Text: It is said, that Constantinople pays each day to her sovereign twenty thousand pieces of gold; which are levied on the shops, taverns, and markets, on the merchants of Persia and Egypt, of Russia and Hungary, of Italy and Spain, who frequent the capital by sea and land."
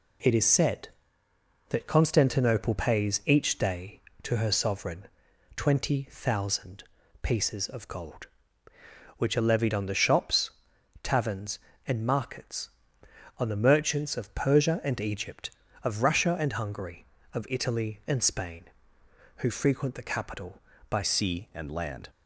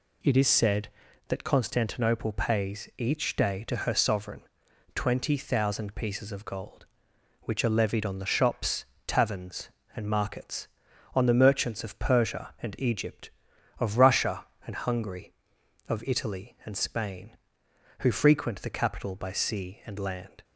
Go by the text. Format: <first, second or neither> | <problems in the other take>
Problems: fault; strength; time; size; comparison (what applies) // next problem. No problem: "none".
second | pauses between "sovereign" and "twenty"; noticeable; at 5.0 s; 0.48 s long; noticeable in the second // pauses between "thousand" and "pieces"; at 6.8 s; 0.40 s long // changes voice at "sea"; from 21.0 s on; 1.0 s long